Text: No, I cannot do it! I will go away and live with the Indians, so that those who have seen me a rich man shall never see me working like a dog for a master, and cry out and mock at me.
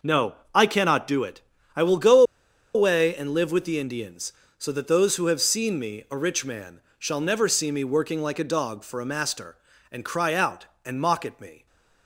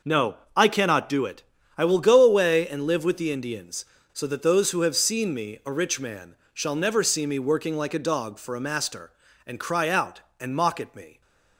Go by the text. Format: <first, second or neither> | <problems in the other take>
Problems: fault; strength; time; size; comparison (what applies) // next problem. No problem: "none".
second | pauses between "go" and "away"; noticeable; at 2.2 s; 0.52 s long // pauses between "man" and "shall"; slight; at 6.7 s; 0.18 s long; slight in the second